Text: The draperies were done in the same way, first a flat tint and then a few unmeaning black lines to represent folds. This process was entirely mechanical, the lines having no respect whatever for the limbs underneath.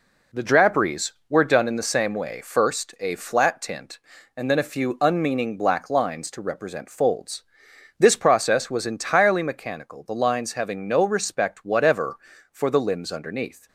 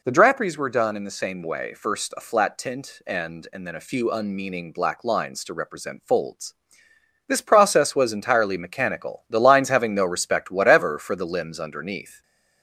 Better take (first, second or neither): first